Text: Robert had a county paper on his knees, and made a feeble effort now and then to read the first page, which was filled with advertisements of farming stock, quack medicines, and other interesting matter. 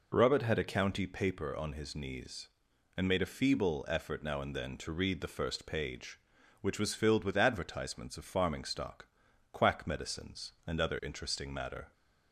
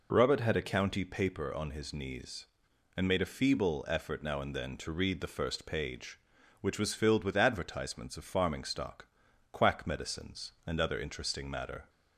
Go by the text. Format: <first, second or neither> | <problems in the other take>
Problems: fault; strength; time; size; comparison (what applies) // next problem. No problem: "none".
neither | none